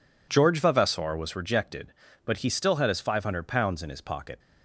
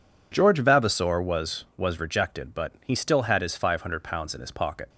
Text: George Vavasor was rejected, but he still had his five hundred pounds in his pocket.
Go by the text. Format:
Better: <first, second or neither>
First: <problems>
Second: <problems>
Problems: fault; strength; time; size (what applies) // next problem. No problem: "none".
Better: first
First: none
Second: says "was" twice; at 1.7 s